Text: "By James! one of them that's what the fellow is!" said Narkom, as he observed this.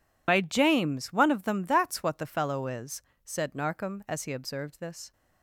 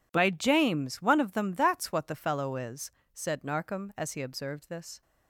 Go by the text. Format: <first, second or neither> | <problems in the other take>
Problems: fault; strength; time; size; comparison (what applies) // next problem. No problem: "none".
second | loses the start of "By"; at 0.2 s; 60 ms